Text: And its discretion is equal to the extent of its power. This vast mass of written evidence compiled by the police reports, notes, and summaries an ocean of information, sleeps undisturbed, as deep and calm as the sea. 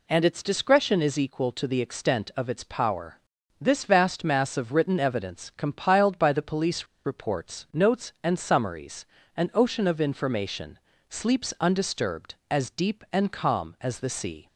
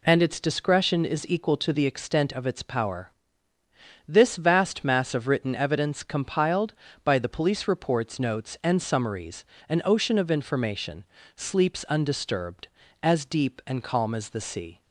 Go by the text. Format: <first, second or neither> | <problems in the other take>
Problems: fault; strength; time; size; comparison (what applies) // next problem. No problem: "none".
second | pauses between "police" and "reports"; slight; at 6.8 s; 0.18 s long // pauses between "summaries" and "an"; slight; at 9.0 s; 0.30 s long; slight in the second